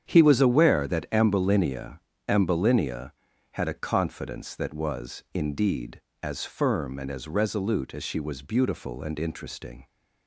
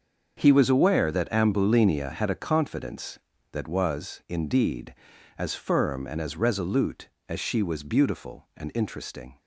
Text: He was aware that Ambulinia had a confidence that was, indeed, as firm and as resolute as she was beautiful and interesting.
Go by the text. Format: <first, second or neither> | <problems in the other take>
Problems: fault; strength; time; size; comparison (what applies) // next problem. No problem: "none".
second | starts louder than the rest; strong; until 1.1 s; 8.5 dB; also in the second // says "Ambulinia" twice; at 2.2 s